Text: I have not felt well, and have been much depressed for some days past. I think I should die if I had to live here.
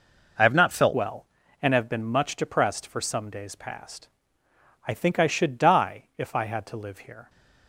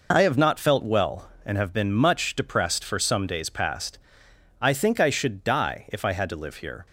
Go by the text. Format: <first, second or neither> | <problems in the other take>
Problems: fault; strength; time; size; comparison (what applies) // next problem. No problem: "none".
second | changes voice at "well"; from 0.9 s on; 6.3 s long